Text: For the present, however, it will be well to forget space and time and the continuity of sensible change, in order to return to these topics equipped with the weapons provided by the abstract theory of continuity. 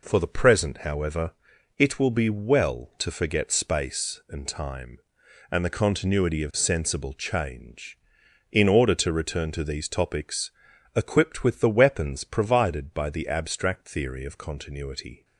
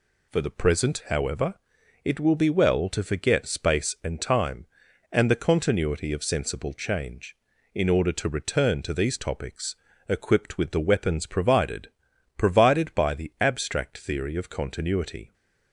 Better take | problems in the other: first | pauses between "topics" and "equipped"; slight; at 9.7 s; 0.34 s long; also in the first // says "provided" twice; at 12.3 s

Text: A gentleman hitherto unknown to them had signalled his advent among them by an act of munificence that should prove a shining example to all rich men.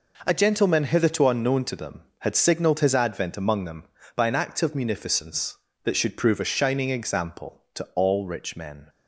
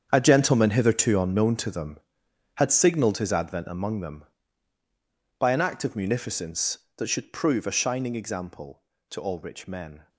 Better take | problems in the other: first | gets quieter; strong; throughout; 14 dB

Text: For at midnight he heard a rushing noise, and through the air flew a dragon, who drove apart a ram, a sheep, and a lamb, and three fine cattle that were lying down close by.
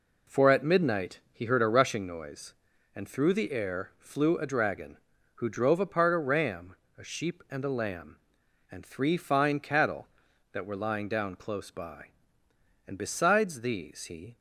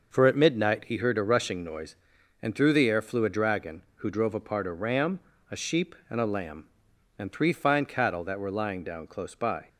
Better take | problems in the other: second | goes on to say "And besides these he"; from 12.8 s on; 1.5 s long

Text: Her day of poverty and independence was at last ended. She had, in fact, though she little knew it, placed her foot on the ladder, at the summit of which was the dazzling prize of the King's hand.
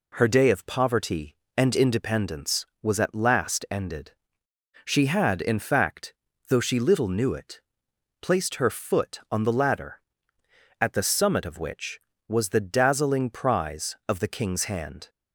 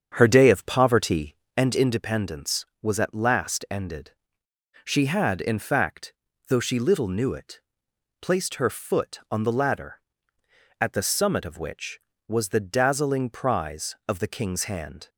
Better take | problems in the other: first | starts louder than the rest; strong; until 1.6 s; 7.5 dB

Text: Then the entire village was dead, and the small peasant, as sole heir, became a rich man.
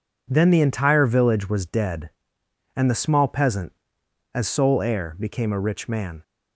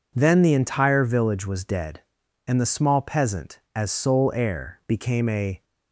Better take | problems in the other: first | stops before "rich man"; at 5.6 s

